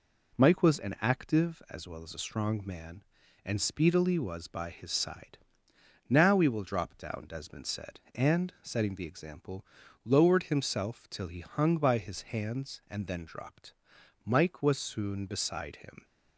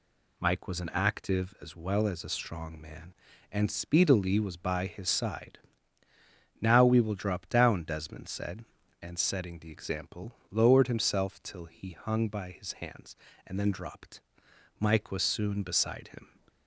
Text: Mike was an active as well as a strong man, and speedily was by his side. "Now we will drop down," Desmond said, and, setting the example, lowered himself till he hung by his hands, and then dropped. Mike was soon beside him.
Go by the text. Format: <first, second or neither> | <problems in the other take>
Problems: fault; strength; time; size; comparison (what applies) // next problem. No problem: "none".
neither | none